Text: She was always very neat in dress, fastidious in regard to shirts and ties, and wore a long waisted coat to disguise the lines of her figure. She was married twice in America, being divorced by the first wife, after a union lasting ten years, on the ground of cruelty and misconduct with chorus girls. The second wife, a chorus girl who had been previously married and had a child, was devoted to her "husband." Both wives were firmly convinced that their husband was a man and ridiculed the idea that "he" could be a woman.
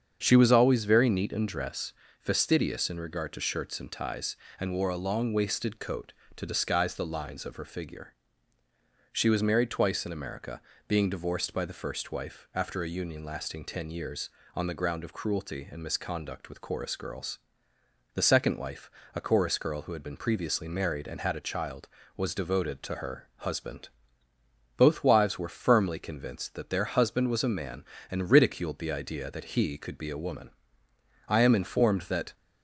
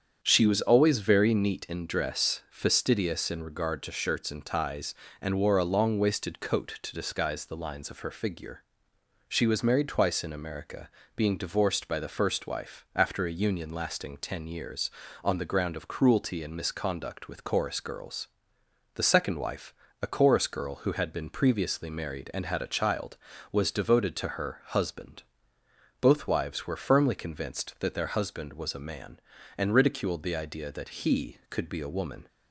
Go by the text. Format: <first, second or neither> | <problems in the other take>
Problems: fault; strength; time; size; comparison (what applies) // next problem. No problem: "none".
second | starts louder than the rest; strong; until 1.2 s; 7.5 dB; strong in the second // goes on to say "I am informed that"; noticeable; from 31.2 s on; 1.0 s long